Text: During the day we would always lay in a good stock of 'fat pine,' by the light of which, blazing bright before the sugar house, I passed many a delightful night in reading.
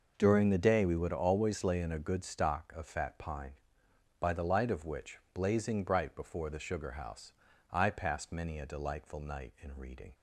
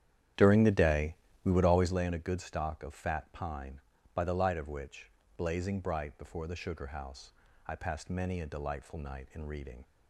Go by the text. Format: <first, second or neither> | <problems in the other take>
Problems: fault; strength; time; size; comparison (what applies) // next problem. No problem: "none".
first | starts louder than the rest; strong; until 2.0 s; 10.5 dB // pauses between "day" and "we"; slight; at 1.1 s; 0.30 s long